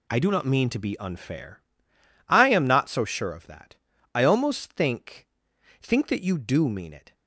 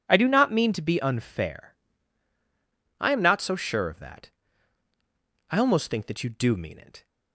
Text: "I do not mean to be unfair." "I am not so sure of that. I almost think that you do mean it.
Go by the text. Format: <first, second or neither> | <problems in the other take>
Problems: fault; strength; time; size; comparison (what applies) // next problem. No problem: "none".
second | says "think" twice; at 5.8 s